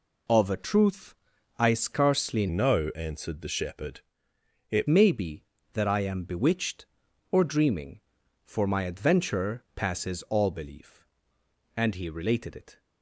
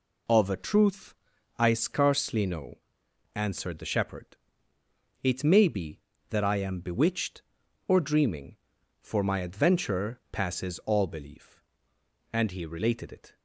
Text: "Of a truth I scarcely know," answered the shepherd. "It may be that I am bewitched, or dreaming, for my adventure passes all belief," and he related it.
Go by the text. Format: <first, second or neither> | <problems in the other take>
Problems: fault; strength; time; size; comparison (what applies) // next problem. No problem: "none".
second | pauses between "truth" and "I"; noticeable; at 1.1 s; 0.46 s long; noticeable in the second // changes voice from "know" to "It"; from 2.4 to 4.8 s; 2.4 s long